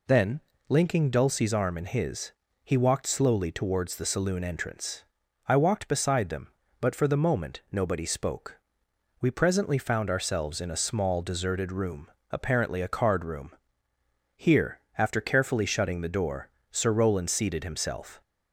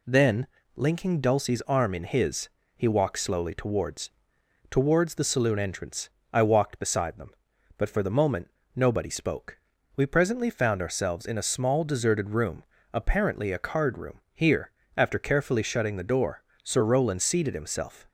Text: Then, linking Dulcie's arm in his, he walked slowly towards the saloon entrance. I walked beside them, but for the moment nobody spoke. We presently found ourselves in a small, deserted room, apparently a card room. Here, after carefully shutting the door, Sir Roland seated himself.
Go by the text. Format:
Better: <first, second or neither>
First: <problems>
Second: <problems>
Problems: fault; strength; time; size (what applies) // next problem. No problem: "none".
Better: first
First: none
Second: says "towards" twice; at 4.7 s // pauses between "moment" and "nobody"; slight; at 8.4 s; 0.24 s long